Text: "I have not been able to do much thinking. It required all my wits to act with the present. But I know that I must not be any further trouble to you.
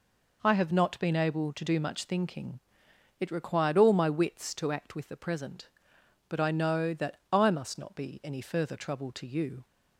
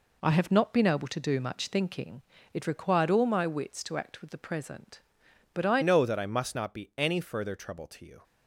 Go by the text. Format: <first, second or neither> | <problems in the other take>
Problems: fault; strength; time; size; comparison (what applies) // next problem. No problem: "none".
first | changes voice at "know"; from 5.8 s on; 2.4 s long